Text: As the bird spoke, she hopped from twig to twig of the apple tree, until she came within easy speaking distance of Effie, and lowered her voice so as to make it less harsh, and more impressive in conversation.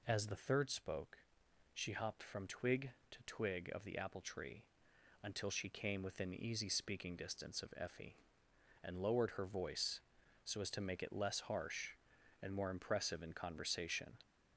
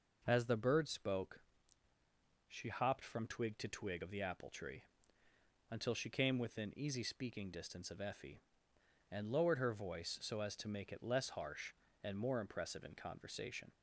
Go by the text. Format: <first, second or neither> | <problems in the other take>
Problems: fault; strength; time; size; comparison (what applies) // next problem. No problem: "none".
second | says "third" for "bird"; at 0.3 s